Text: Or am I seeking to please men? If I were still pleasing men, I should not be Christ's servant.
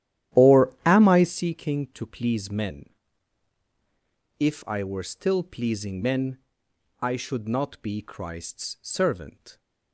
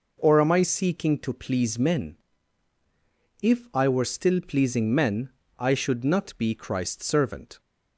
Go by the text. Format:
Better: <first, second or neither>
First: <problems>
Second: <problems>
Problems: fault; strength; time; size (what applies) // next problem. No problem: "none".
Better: second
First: starts louder than the rest; strong; until 1.4 s; 11.5 dB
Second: none